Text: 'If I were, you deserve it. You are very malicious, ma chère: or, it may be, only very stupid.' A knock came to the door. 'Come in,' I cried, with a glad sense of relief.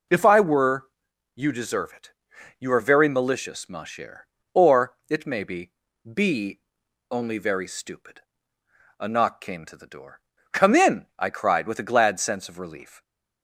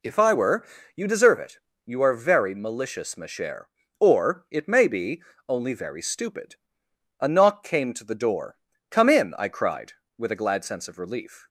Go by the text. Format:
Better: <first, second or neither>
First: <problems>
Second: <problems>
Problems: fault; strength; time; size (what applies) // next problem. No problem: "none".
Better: second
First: says "be" twice; at 6.1 s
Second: none